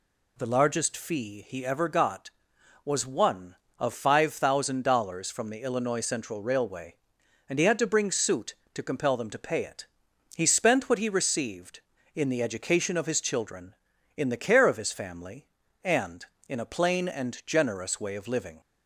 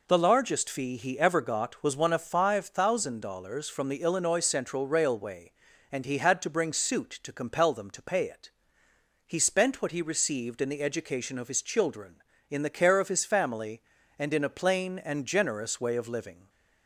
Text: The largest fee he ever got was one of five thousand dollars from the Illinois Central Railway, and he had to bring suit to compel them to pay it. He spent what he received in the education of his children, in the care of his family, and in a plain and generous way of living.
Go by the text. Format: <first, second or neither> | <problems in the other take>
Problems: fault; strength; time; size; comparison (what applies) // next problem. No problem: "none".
neither | none